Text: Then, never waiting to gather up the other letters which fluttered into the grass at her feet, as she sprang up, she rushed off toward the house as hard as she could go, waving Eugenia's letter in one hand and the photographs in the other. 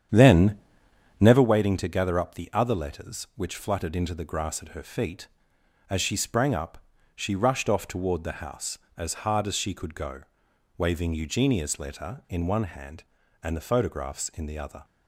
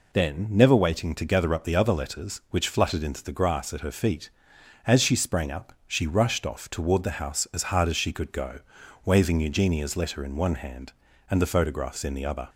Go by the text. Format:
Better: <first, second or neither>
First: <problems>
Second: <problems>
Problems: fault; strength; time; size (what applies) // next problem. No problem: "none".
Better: second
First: starts louder than the rest; strong; until 1.4 s; 9 dB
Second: none